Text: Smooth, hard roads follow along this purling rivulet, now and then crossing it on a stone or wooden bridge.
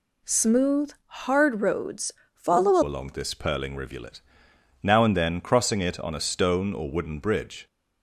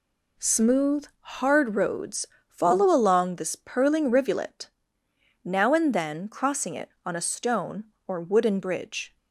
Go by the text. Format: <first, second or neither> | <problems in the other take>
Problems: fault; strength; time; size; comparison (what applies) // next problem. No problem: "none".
second | pauses between "roads" and "follow"; slight; at 2.0 s; 0.24 s long; slight in the second // changes voice at "along"; from 2.8 s on; 4.8 s long